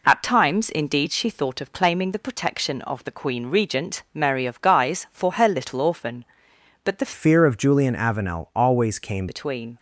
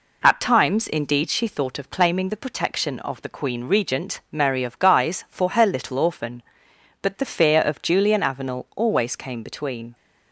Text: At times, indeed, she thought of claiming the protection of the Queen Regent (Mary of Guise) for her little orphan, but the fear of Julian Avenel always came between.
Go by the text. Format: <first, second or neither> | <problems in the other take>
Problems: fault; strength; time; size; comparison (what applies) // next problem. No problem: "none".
second | changes voice from "fear" to "came"; from 7.1 to 9.2 s; 2.1 s long